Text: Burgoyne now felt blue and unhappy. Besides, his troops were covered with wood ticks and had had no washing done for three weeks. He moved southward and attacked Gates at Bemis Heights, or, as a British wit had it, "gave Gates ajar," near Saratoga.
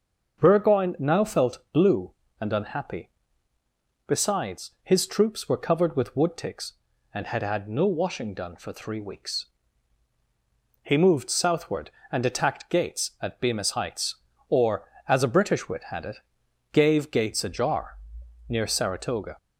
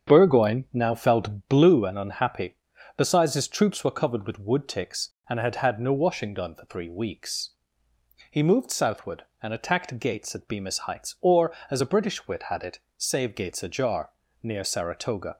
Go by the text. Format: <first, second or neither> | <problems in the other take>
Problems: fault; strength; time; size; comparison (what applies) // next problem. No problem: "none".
first | starts louder than the rest; strong; until 1.1 s; 7.5 dB; also in the first // says "save" for "gave"; at 12.9 s